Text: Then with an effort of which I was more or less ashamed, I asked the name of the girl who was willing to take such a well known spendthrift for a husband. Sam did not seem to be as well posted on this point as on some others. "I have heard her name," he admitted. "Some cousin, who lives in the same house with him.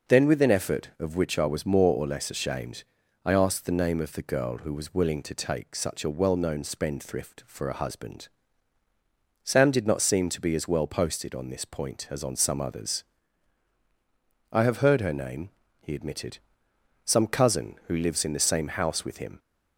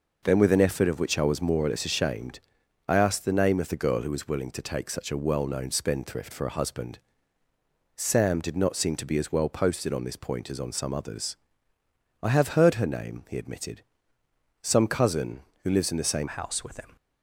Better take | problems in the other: first | changes voice at "house"; from 16.2 s on; 0.7 s long

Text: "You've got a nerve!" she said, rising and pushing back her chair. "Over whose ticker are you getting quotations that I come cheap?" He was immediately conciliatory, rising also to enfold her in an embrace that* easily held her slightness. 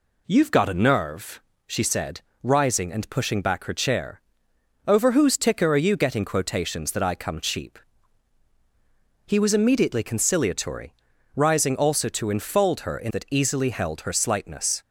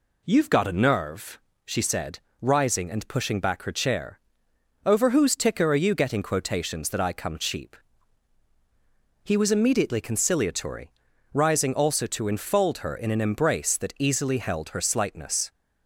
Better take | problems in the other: second | skips "an embrace"; at 13.1 s

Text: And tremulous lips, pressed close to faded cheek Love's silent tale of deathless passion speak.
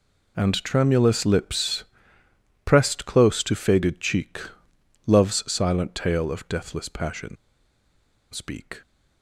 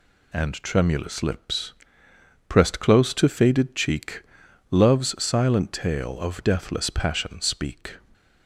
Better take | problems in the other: second | pauses between "cheek" and "Love's"; noticeable; at 4.3 s; 0.68 s long; noticeable in the second // pauses between "passion" and "speak"; noticeable; at 7.3 s; 0.97 s long

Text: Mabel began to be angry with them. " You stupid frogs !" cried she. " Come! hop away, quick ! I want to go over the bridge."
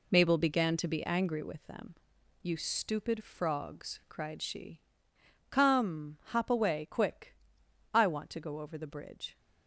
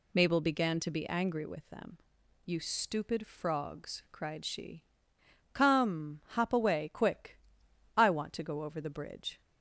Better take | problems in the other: second | gets quieter; throughout; 6.5 dB

